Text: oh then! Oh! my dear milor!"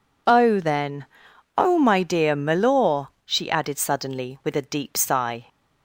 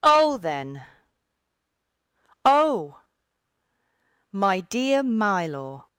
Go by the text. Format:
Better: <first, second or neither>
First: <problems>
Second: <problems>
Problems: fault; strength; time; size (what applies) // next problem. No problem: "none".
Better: second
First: goes on to say "she added suddenly with a deep sigh"; strong; from 3.2 s on; 2.2 s long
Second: none